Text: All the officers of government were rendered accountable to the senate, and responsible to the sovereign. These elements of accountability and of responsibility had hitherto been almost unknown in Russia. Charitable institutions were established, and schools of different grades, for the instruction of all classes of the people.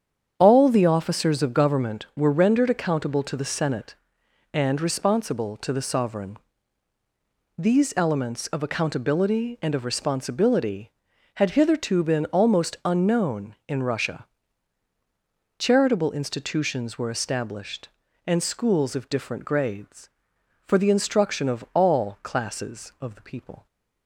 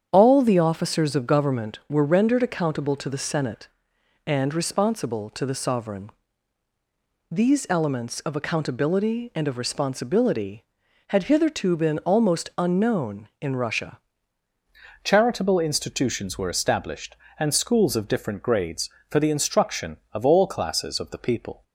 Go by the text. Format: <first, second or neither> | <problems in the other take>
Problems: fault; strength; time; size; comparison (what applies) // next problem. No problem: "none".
first | starts louder than the rest; strong; until 1.1 s; 8 dB; strong in the first // changes voice at "Charitable"; from 15.0 s on; 6.6 s long